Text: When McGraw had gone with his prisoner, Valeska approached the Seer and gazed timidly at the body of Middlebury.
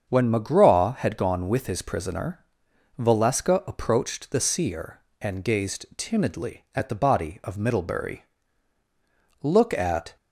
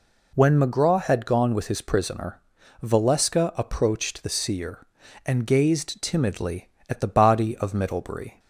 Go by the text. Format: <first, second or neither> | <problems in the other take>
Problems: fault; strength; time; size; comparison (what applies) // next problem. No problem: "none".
second | starts louder than the rest; strong; until 1.1 s; 7 dB // goes on to say "Look at"; noticeable; from 9.4 s on; 0.74 s long